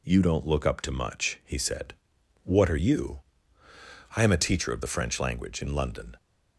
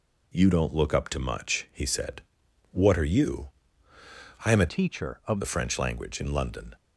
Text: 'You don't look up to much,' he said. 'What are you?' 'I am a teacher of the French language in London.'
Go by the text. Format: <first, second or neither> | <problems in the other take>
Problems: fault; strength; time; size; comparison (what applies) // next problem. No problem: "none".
first | changes voice from "teacher" to "of"; from 4.6 to 5.3 s; 0.7 s long